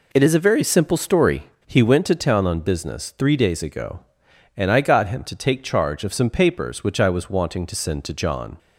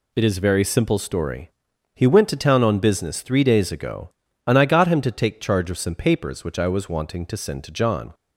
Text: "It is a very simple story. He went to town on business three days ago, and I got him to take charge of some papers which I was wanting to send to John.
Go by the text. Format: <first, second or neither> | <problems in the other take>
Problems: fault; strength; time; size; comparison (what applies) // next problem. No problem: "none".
neither | none